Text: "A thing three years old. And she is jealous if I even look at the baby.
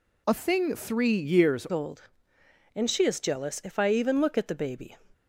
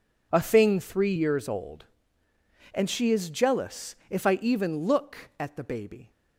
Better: second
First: changes voice at "old"; from 1.7 s on; 3.2 s long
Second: none

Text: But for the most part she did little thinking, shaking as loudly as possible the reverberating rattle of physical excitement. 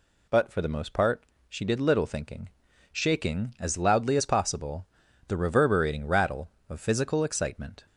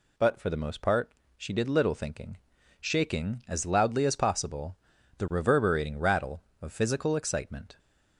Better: neither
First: pauses between "part" and "she"; slight; at 1.2 s; 0.24 s long // pauses between "possible" and "the"; at 4.8 s; 0.42 s long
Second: pauses between "part" and "she"; slight; at 1.1 s; 0.24 s long // pauses between "possible" and "the"; at 4.7 s; 0.42 s long

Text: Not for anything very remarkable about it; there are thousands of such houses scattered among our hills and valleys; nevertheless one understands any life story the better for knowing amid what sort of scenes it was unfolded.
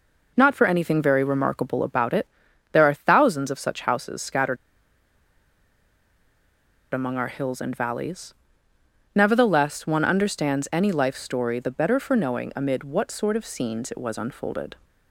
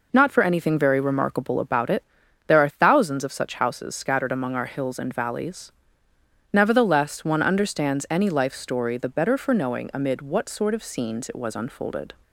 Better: second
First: pauses between "scattered" and "among"; strong; at 4.5 s; 2.3 s long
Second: none

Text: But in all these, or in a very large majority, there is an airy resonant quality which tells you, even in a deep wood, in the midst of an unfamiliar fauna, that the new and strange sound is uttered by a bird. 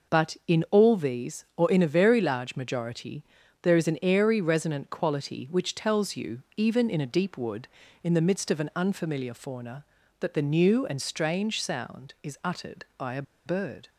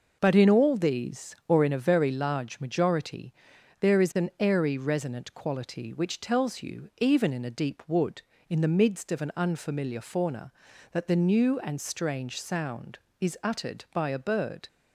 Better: second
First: pauses between "a" and "bird"; slight; at 13.2 s; 0.23 s long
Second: none

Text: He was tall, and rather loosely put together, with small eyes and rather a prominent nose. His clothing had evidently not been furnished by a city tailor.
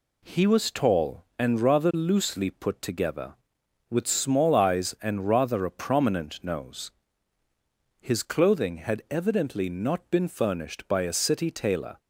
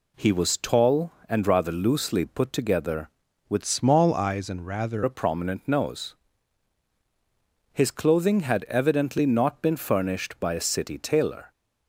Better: first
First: none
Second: changes voice from "small" to "rather"; from 3.6 to 5.0 s; 1.4 s long

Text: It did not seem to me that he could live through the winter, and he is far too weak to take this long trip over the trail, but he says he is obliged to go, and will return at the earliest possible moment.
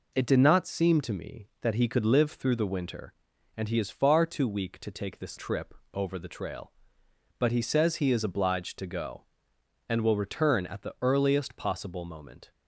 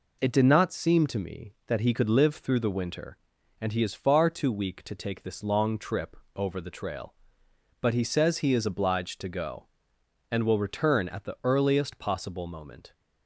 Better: second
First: skips "long"; at 5.3 s // pauses between "trip" and "over"; slight; at 5.7 s; 0.18 s long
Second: pauses between "trip" and "over"; slight; at 6.1 s; 0.18 s long

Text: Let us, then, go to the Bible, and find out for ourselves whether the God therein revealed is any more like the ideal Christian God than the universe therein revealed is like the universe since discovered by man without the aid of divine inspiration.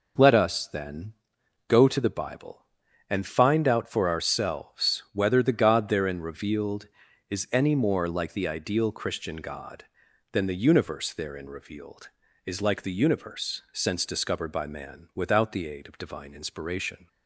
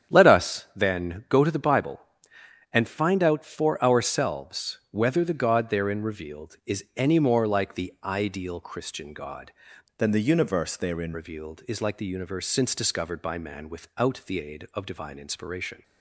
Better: first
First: none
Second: starts louder than the rest; strong; until 1.2 s; 9 dB // changes voice from "than" to "therein"; from 9.9 to 11.1 s; 1.2 s long

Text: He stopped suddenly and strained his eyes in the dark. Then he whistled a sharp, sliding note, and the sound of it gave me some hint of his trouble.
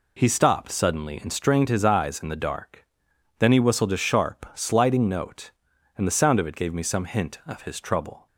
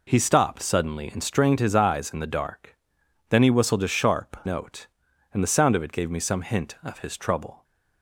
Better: first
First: none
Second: skips "sliding"; at 4.4 s

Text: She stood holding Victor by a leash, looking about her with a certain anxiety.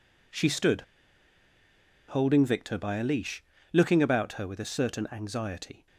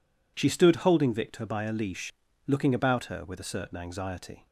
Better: second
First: pauses between "stood" and "holding"; strong; at 0.7 s; 1.3 s long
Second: none

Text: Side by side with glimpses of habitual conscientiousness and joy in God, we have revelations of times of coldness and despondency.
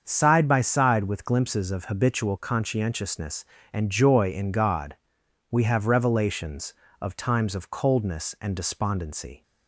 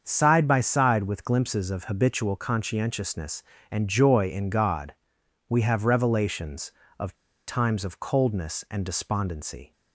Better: first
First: starts louder than the rest; until 1.0 s; 7 dB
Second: starts louder than the rest; until 1.0 s; 7 dB // pauses between "of" and "times"; slight; at 7.1 s; 0.33 s long

